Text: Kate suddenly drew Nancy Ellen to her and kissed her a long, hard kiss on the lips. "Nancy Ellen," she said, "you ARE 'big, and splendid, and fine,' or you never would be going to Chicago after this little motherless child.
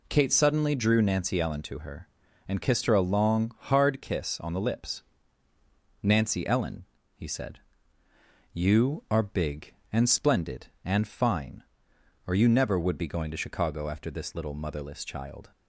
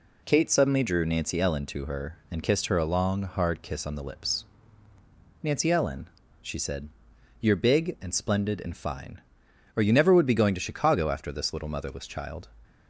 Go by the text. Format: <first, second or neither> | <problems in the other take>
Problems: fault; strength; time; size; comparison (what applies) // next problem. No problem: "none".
second | says "he" for "she"; at 7.1 s